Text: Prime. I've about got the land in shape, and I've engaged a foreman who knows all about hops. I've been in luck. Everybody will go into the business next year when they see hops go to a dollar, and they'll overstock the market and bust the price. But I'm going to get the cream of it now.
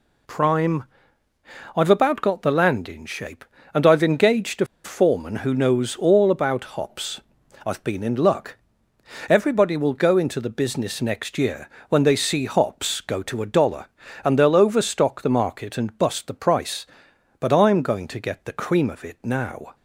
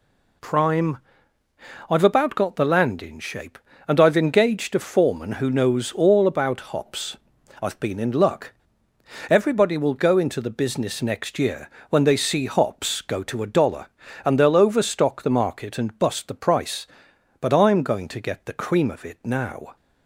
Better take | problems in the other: second | pauses between "a" and "foreman"; slight; at 4.6 s; 0.18 s long // pauses between "year" and "when"; slight; at 11.6 s; 0.22 s long; slight in the second

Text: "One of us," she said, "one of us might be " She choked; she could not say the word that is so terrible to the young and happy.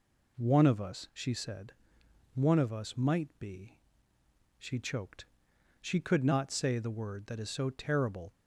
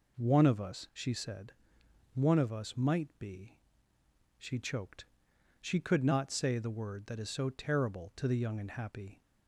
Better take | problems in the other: second | stops before "to the young and happy"; at 8.3 s

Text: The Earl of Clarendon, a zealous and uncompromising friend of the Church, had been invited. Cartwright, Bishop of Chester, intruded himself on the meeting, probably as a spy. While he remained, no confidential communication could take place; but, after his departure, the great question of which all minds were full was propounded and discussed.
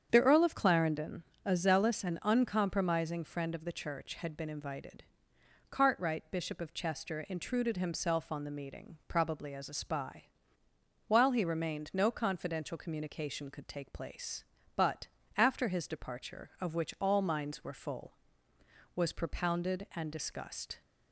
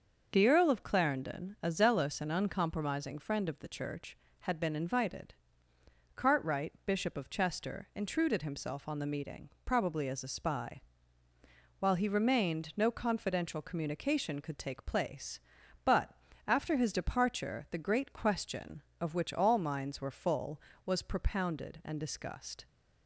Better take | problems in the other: second | starts louder than the rest; strong; until 1.1 s; 7.5 dB // skips "the great question"; at 16.5 s

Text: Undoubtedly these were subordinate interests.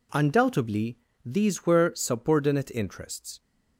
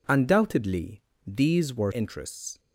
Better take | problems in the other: first | pauses between "Undoubtedly" and "these"; slight; at 0.9 s; 0.26 s long; slight in the first // skips "subordinate"; at 1.9 s

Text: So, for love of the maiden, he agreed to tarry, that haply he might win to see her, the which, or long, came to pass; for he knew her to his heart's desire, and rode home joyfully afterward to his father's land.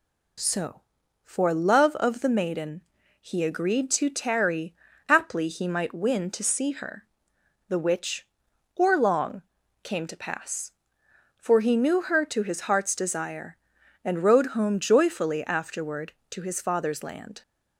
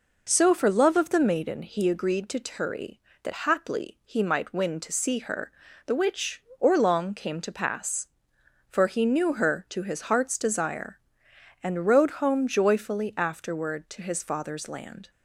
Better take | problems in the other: second | skips "that"; at 4.9 s

